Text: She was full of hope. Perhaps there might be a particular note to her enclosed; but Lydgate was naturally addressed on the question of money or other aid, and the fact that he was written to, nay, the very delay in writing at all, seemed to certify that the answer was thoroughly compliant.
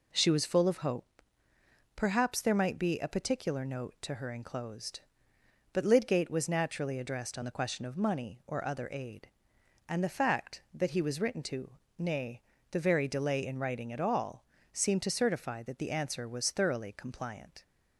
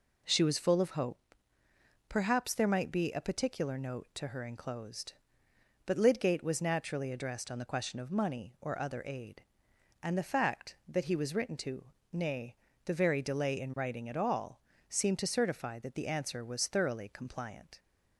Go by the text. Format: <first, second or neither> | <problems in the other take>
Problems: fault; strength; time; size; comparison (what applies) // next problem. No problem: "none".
neither | none